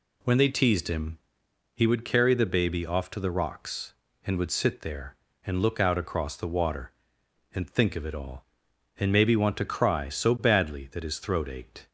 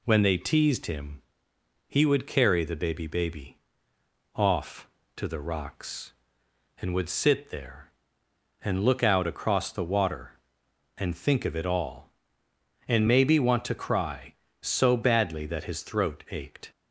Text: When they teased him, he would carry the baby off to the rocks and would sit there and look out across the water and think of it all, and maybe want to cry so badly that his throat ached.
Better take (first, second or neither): first